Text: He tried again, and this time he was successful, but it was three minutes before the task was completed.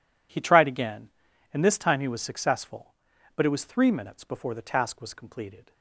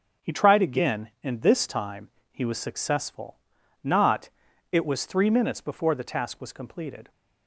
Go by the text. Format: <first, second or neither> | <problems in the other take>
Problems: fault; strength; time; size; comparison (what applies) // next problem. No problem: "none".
first | pauses between "time" and "he"; slight; at 2.0 s; 0.22 s long // says "not" for "but"; at 3.8 s